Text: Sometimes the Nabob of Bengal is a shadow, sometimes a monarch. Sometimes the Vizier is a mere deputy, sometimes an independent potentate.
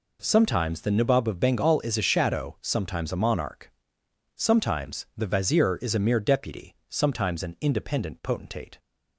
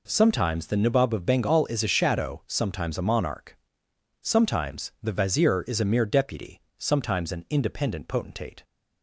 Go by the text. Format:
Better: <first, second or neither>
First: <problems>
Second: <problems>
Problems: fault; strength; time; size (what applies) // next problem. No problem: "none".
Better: neither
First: none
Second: none